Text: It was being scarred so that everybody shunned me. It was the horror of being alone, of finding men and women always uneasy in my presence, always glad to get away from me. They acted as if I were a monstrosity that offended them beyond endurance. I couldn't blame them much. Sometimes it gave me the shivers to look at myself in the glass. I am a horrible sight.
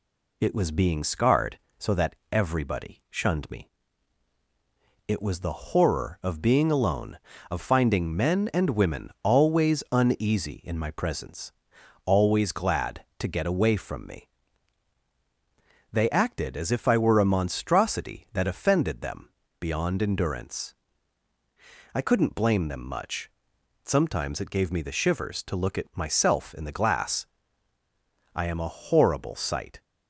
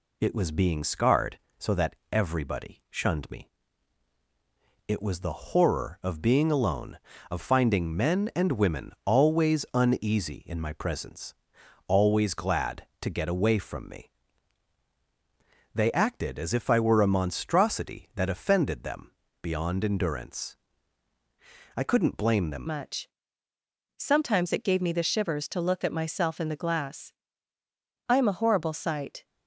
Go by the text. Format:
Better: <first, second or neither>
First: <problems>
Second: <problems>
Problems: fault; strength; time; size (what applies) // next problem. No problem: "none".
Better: first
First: pauses between "that" and "everybody"; slight; at 2.1 s; 0.16 s long // pauses between "them" and "beyond"; slight; at 19.2 s; 0.32 s long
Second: pauses between "that" and "everybody"; slight; at 1.9 s; 0.16 s long // pauses between "them" and "beyond"; slight; at 19.1 s; 0.32 s long // changes voice at "much"; from 22.6 s on; 6.6 s long